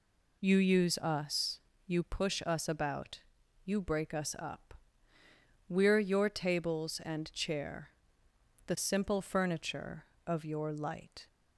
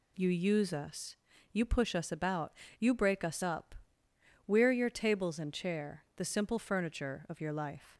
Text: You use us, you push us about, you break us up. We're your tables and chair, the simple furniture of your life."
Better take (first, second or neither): second